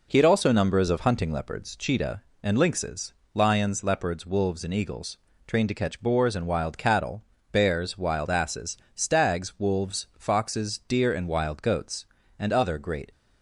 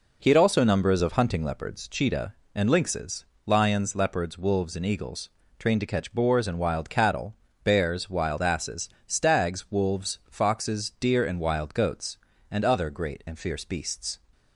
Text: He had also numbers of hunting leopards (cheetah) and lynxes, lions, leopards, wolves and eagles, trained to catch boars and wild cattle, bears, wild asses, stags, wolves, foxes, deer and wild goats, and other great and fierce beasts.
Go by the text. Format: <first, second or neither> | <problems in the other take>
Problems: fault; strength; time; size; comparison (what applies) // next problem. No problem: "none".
second | stops before "and fierce beasts"; at 13.1 s